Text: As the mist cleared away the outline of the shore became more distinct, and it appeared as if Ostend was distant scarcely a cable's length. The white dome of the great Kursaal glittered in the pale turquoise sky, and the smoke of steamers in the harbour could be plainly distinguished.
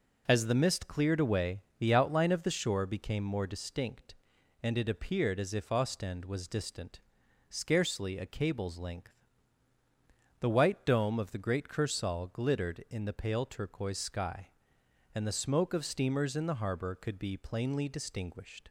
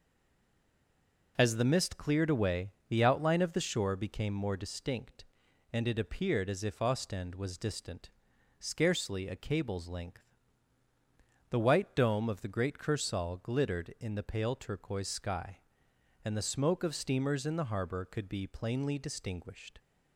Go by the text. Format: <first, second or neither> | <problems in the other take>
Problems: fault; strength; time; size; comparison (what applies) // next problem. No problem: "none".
first | stays silent before the first word; noticeable; until 1.3 s; 1.3 s long // pauses between "away" and "the"; slight; at 2.7 s; 0.18 s long; slight in the first // pauses between "distant" and "scarcely"; noticeable; at 8.1 s; 0.48 s long; noticeable in the first